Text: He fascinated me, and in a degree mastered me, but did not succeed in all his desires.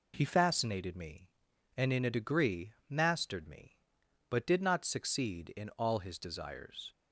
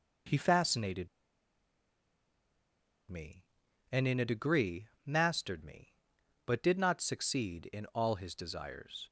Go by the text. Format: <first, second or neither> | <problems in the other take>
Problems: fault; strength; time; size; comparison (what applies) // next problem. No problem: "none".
first | pauses between "fascinated" and "me"; strong; at 1.0 s; 2.0 s long // pauses between "degree" and "mastered"; slight; at 4.8 s; 0.18 s long; slight in the first